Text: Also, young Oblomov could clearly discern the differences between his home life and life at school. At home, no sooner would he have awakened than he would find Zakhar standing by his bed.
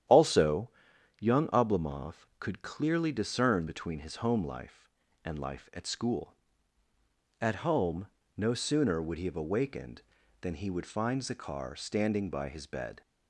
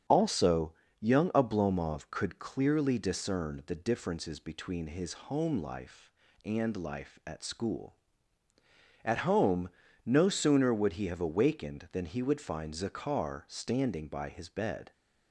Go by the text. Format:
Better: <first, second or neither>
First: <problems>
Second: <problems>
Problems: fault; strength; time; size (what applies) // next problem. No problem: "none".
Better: second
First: starts louder than the rest; strong; until 1.6 s; 10.5 dB // skips "the differences"; at 3.6 s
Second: starts louder than the rest; strong; until 1.3 s; 8 dB